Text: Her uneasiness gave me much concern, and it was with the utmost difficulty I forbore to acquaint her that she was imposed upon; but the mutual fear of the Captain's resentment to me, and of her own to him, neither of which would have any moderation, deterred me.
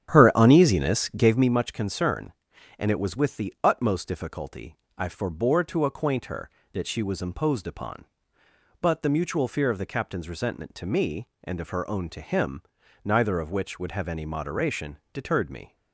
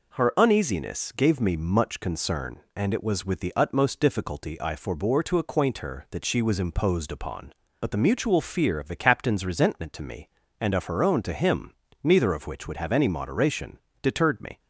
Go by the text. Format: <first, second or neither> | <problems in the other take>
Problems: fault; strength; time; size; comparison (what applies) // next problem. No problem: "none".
second | starts louder than the rest; strong; until 1.6 s; 10 dB // pauses between "difficulty" and "I"; slight; at 4.7 s; 0.22 s long